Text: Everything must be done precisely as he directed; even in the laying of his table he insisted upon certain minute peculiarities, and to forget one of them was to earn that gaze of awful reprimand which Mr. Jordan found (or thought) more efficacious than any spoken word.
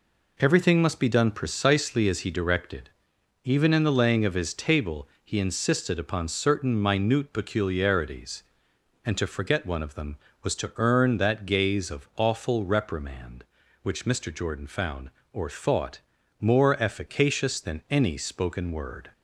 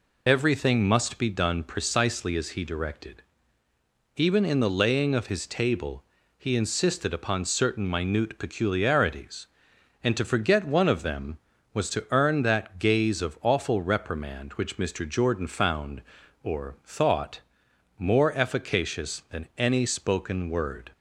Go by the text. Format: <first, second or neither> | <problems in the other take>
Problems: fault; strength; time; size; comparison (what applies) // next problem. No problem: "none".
first | loses the start of "Everything"; at 0.2 s; 60 ms // pauses between "table" and "he"; slight; at 6.0 s; 0.32 s long; slight in the first